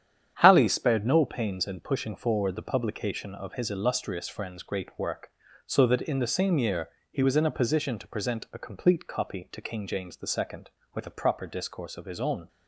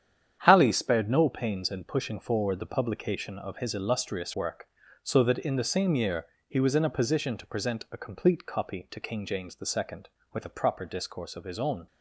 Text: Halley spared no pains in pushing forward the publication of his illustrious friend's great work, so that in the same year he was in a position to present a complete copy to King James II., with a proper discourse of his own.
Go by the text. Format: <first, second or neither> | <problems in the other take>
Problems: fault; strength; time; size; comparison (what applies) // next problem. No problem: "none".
first | starts louder than the rest; strong; until 1.4 s; 9 dB; strong in the first // skips "friend's great"; at 4.3 s // pauses between "year" and "he"; slight; at 6.2 s; 0.22 s long; slight in the first